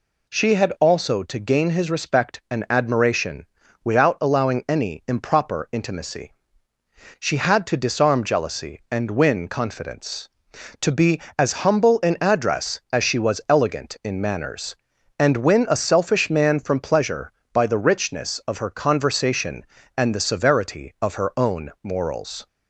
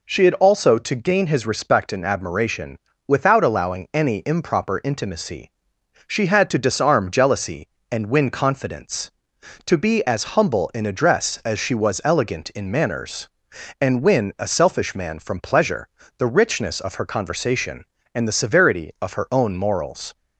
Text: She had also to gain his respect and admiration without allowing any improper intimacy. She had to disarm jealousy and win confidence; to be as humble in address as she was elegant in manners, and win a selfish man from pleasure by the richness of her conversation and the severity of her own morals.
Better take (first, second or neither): first